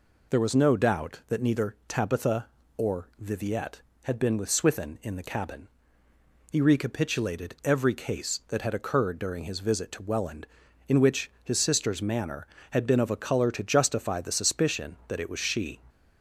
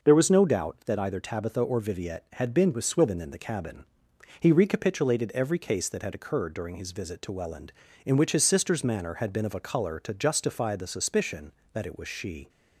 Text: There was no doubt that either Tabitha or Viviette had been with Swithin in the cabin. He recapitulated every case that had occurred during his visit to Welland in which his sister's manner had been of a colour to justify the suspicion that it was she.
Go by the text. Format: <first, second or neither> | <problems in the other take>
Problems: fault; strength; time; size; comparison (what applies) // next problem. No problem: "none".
second | says "neither" for "either"; at 1.4 s